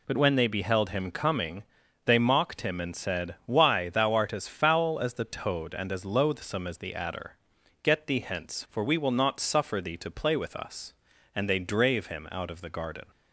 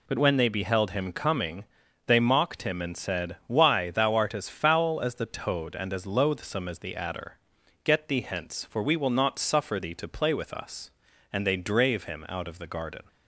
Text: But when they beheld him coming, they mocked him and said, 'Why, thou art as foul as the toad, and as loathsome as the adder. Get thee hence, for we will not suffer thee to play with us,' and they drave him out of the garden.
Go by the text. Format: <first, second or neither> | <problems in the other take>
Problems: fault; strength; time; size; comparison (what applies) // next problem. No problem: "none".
neither | none